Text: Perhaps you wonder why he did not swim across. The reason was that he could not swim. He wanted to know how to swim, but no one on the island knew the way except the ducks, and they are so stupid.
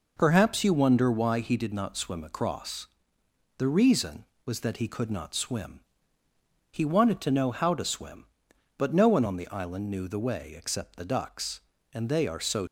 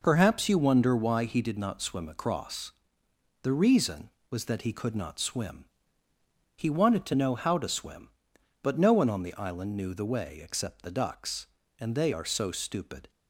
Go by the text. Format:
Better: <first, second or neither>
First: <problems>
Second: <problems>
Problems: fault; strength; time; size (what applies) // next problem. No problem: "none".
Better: second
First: stops before "stupid"; at 12.6 s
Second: none